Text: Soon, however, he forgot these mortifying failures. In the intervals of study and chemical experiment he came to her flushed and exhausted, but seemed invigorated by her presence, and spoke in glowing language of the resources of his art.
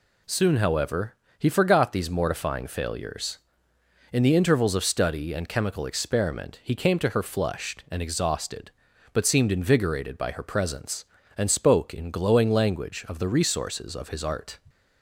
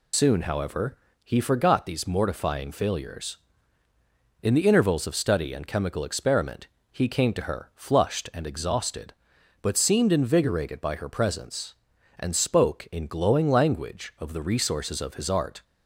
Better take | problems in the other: first | loses the start of "Soon"; at 0.1 s; 85 ms // pauses between "experiment" and "he"; slight; at 6.6 s; 0.24 s long

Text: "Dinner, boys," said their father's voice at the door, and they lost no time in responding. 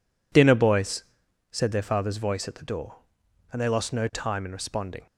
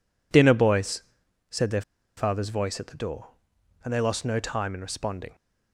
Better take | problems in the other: first | pauses between "their" and "father's"; slight; at 1.8 s; 0.35 s long

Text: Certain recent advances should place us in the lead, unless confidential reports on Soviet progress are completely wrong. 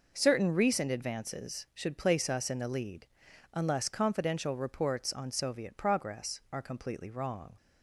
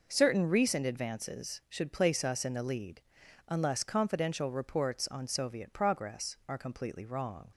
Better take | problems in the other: neither | none

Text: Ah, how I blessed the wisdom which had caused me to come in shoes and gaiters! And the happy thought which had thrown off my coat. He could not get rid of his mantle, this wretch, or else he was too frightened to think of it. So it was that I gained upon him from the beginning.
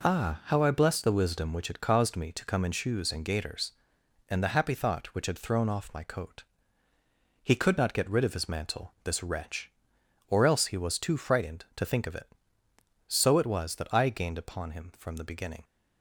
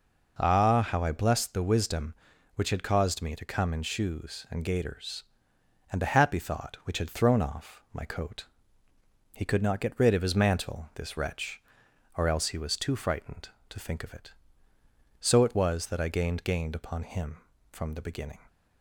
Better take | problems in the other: first | says "gained" twice; at 16.4 s

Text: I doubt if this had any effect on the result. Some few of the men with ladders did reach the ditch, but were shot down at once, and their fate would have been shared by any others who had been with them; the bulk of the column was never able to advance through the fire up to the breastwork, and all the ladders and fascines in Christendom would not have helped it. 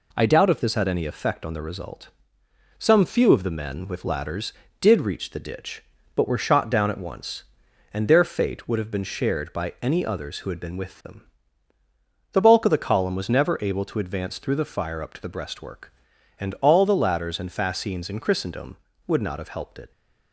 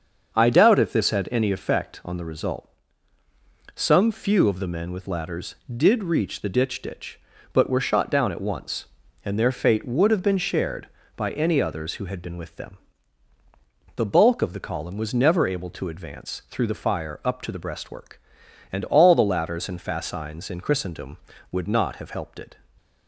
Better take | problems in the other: first | starts louder than the rest; until 1.3 s; 6.5 dB // says "ditch" twice; at 6.8 s

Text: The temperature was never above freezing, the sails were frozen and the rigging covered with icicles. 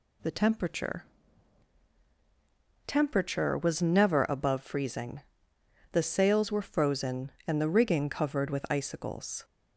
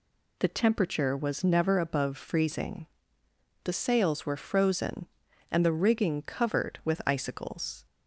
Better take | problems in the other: second | says "temperature" twice; at 2.8 s

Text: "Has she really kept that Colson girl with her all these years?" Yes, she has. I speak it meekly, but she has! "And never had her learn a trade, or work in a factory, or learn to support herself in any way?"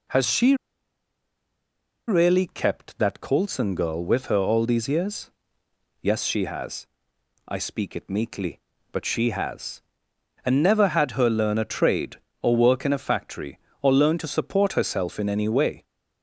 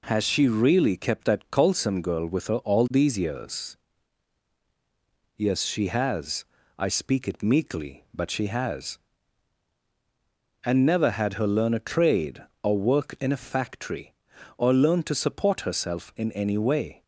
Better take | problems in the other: second | pauses between "she" and "really"; strong; at 0.5 s; 1.5 s long

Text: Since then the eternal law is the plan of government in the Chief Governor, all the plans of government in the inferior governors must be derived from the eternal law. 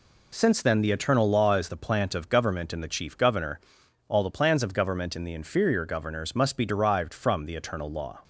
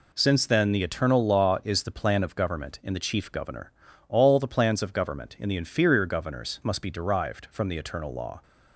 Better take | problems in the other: second | says "plant" for "plan"; at 1.7 s

